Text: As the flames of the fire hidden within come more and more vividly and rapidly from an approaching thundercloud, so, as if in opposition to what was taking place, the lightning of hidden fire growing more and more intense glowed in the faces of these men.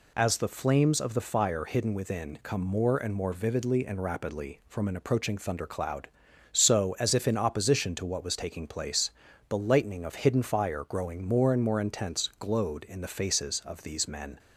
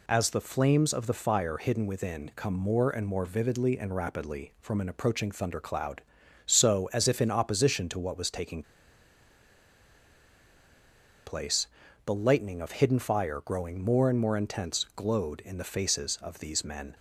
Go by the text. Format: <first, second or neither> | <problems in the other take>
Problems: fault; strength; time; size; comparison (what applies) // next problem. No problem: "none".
first | pauses between "taking" and "place"; strong; at 8.6 s; 2.6 s long